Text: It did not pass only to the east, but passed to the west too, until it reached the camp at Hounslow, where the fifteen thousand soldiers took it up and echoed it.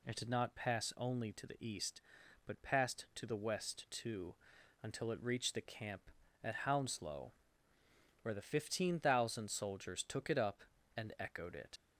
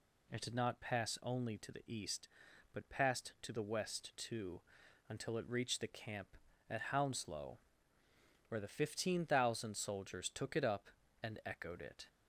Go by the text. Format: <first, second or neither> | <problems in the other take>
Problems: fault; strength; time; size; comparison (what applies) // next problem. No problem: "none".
second | leaves "it" unfinished; at 11.7 s; 50 ms